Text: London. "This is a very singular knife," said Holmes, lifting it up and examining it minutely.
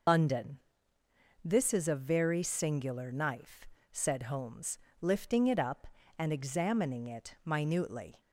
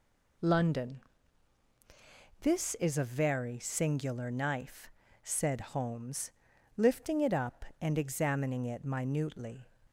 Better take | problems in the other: second | loses the start of "London"; at 0.0 s; 75 ms

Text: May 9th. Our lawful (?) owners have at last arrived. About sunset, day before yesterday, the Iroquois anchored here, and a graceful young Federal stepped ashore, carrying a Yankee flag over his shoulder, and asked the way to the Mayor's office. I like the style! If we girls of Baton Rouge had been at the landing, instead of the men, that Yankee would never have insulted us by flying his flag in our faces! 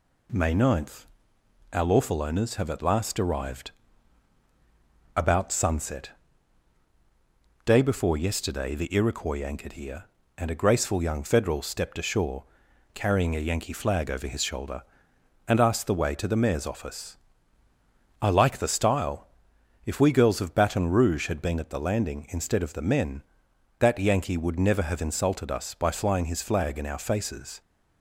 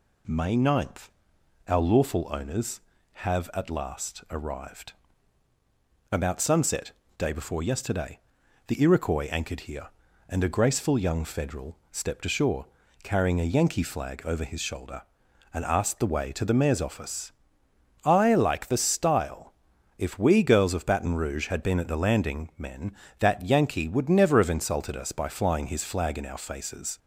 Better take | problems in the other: first | skips "instead of the"; at 22.5 s

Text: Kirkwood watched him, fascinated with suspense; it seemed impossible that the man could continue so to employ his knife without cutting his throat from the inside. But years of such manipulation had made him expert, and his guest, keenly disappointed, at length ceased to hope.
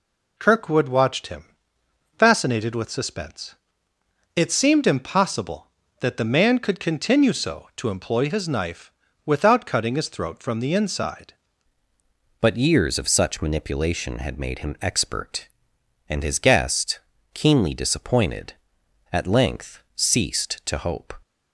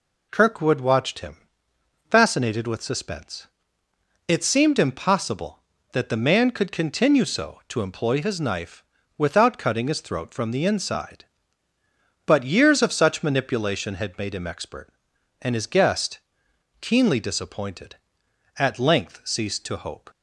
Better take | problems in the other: second | pauses between "knife" and "without"; slight; at 8.9 s; 0.34 s long; slight in the second // changes voice at "But"; from 12.4 s on; 8.7 s long

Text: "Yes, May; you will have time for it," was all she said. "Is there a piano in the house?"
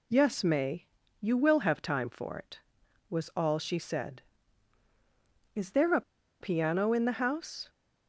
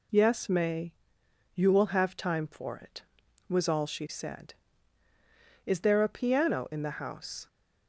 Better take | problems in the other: second | pauses between "a" and "piano"; at 6.0 s; 0.39 s long

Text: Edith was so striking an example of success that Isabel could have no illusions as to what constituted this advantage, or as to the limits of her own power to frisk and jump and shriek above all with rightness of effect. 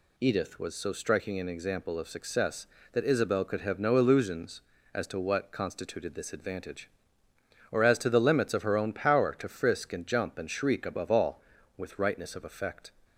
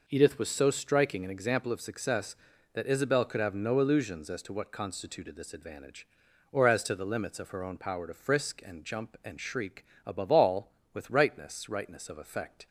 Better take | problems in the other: first | pauses between "shriek" and "above"; slight; at 9.8 s; 0.20 s long // says "rightness" twice; at 11.6 s

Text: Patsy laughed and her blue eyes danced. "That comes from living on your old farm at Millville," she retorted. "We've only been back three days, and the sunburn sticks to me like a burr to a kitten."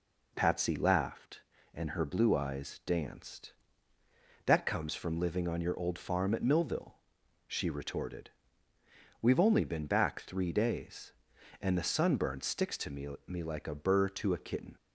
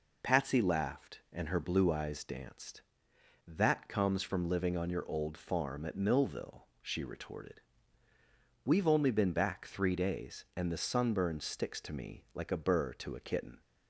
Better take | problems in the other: second | says "me" twice; at 13.2 s

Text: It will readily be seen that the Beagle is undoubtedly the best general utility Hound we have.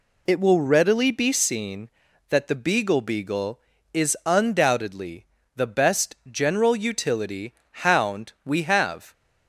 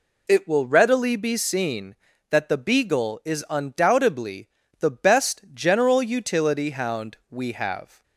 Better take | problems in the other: second | says "Beagle" twice; at 3.0 s // pauses between "undoubtedly" and "the"; slight; at 5.2 s; 0.30 s long; slight in the second // pauses between "utility" and "Hound"; slight; at 7.5 s; 0.28 s long

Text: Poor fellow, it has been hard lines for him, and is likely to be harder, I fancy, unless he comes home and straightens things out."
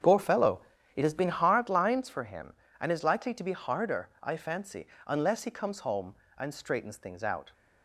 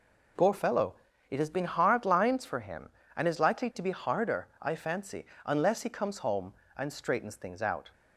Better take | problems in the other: second | starts louder than the rest; strong; until 1.6 s; 7.5 dB

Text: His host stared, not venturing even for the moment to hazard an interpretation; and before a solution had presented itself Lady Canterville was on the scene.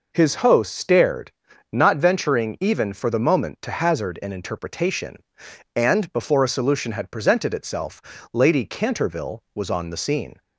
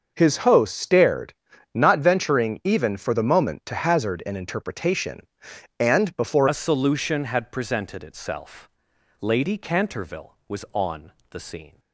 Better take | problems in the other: first | starts louder than the rest; until 1.1 s; 6.5 dB // changes voice at "a"; from 6.4 s on; 5.3 s long // pauses between "itself" and "Lady"; noticeable; at 8.6 s; 0.50 s long; slight in the first // pauses between "on" and "the"; slight; at 11.1 s; 0.20 s long

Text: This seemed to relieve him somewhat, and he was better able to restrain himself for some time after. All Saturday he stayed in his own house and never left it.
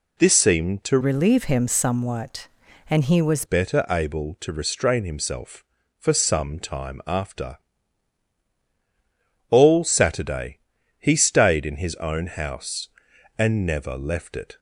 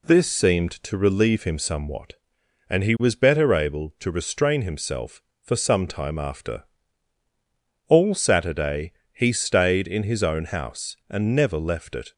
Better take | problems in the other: second | changes voice from "relieve" to "was"; from 1.0 to 3.4 s; 2.4 s long // pauses between "Saturday" and "he"; at 10.5 s; 0.40 s long; slight in the second

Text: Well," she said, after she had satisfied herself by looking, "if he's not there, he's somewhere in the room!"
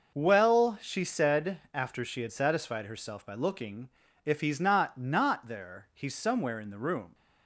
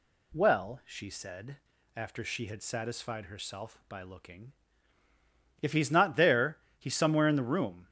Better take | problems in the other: second | says "not" twice; at 4.9 s

